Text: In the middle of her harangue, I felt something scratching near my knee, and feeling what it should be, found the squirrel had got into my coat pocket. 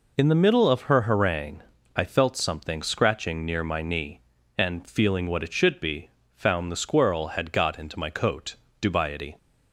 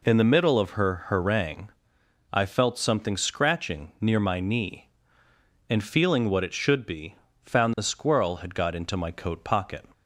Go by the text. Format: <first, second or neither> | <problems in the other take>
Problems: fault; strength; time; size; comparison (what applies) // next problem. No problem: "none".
second | says "dubiety" for "pocket"; at 8.7 s